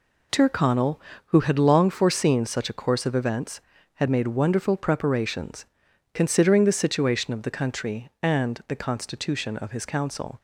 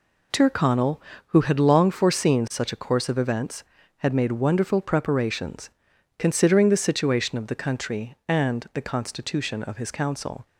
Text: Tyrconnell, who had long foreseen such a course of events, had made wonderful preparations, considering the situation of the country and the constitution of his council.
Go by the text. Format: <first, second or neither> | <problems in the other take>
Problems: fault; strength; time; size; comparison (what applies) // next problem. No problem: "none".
neither | none